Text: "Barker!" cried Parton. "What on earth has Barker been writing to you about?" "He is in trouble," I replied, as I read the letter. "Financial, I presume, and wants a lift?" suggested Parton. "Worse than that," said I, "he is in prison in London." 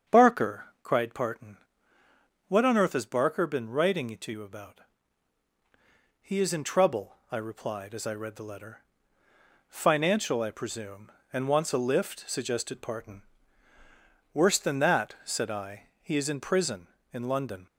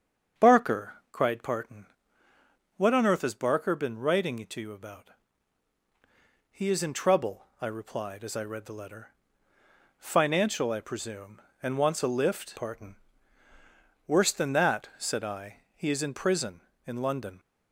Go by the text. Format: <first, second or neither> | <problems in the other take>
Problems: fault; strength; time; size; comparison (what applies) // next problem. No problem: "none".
first | starts louder than the rest; strong; until 1.5 s; 7.5 dB; strong in the first // skips "suggested"; at 12.5 s